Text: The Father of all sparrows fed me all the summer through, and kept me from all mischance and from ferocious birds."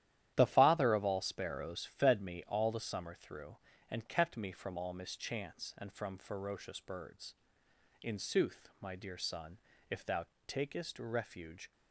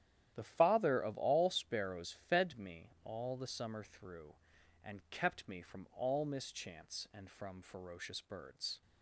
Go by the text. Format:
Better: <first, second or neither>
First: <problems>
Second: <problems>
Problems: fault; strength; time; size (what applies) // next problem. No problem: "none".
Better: second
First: starts louder than the rest; strong; until 1.3 s; 12 dB // goes on to say "In sooth my dear son if thou takest refuge"; strong; from 8.0 s on; 3.6 s long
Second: starts louder than the rest; strong; until 1.3 s; 11 dB